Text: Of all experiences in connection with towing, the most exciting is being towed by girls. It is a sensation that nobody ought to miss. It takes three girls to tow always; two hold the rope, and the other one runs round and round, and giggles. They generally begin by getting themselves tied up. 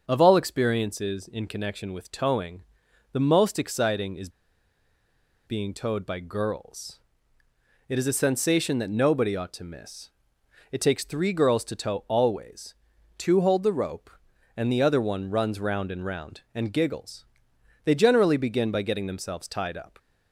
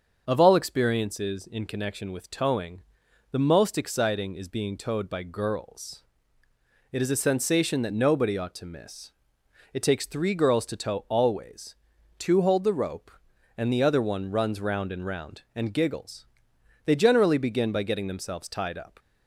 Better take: second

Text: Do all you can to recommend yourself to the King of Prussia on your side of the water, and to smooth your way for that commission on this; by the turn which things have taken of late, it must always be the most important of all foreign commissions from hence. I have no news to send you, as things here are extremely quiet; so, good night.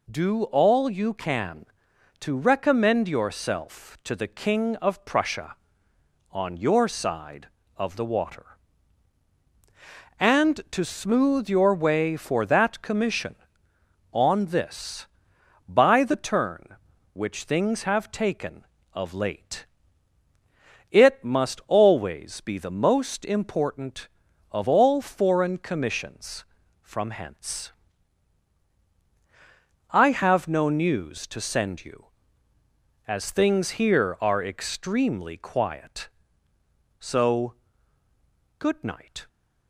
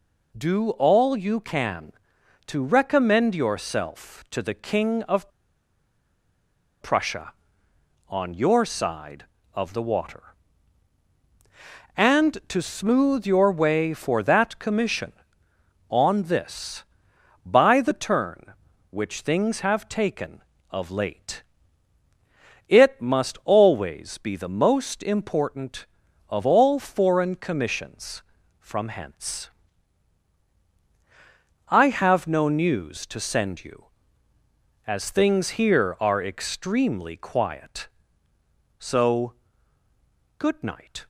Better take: first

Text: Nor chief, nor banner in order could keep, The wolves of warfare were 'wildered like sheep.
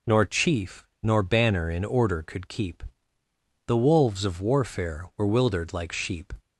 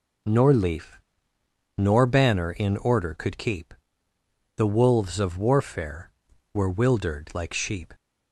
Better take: first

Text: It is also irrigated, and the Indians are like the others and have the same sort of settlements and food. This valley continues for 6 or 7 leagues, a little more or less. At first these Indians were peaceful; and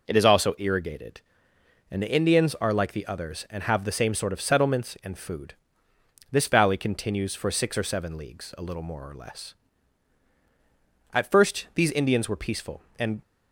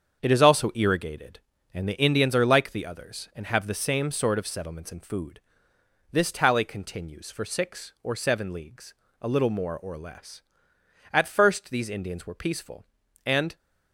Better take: first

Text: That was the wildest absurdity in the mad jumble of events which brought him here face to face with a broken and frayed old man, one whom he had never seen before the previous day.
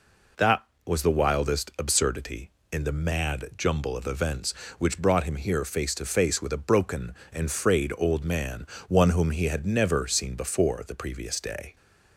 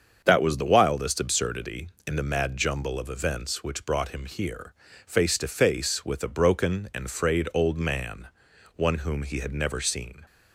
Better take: first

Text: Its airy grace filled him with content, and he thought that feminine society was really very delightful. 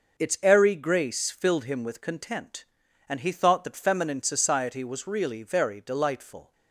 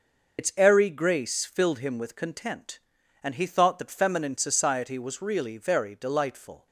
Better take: first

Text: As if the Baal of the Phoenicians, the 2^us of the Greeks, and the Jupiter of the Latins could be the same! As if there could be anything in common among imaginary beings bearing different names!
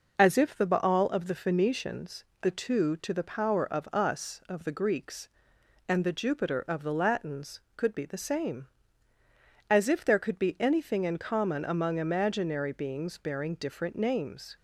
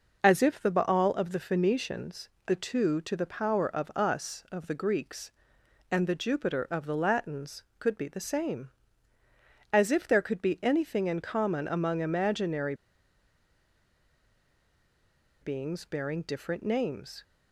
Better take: first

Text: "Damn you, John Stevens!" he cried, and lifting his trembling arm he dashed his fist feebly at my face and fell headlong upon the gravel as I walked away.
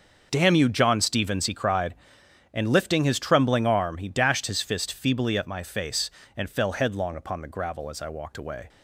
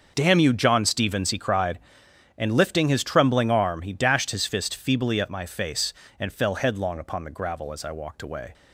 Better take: neither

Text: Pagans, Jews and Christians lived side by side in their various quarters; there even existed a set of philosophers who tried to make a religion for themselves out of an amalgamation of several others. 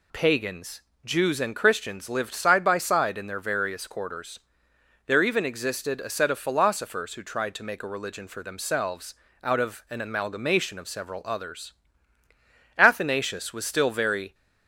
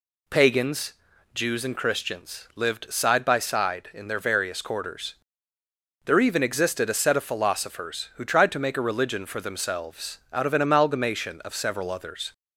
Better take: second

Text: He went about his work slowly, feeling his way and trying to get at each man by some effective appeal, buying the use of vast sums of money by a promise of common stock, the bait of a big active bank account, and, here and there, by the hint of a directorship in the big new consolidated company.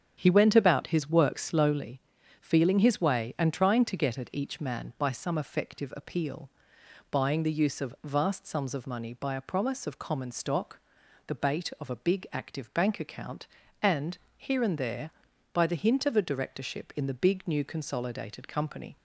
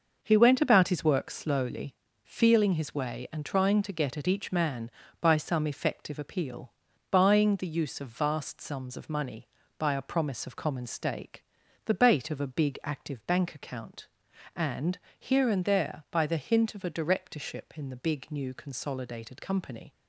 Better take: first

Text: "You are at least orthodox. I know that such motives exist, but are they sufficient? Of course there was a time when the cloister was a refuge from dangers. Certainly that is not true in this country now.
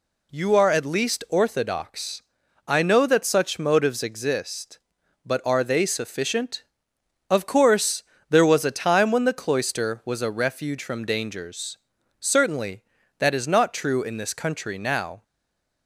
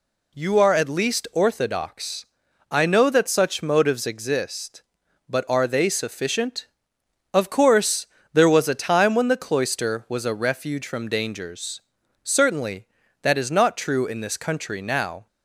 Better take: second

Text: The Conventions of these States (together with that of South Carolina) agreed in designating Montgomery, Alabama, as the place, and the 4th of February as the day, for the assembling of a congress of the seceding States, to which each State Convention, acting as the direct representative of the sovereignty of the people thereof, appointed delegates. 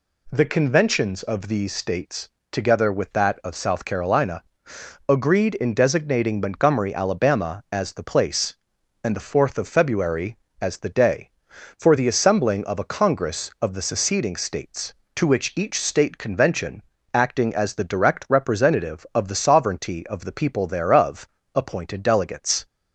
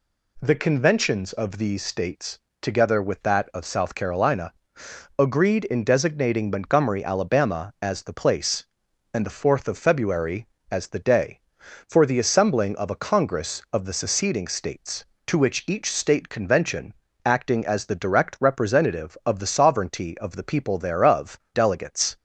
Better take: first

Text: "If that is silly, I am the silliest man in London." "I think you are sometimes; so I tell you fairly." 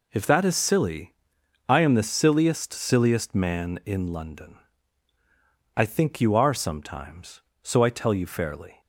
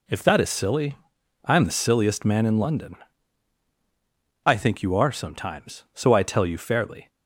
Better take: second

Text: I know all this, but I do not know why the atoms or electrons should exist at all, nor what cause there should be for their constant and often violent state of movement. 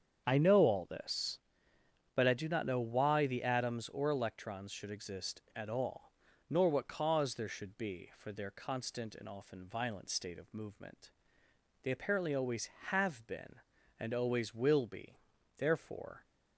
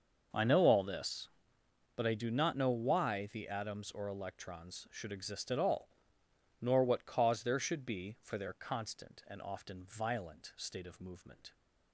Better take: second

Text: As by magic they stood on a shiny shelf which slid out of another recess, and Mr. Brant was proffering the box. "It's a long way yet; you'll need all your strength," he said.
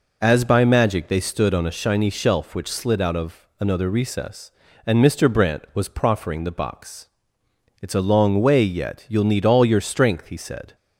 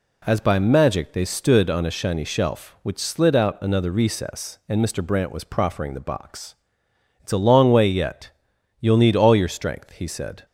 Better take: first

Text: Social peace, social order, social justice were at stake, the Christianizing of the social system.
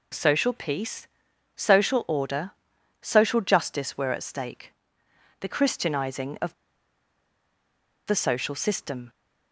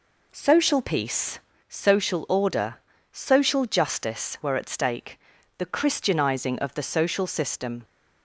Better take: second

